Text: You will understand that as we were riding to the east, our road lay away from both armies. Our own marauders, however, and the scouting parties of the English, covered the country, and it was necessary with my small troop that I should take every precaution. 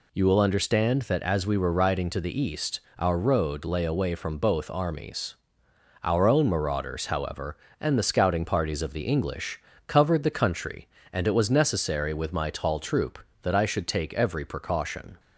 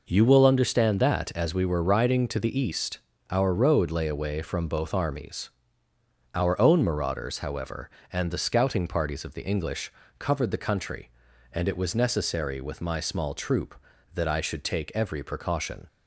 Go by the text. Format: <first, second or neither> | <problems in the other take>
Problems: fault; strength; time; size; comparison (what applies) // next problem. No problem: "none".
second | says "tall" for "small"; at 12.4 s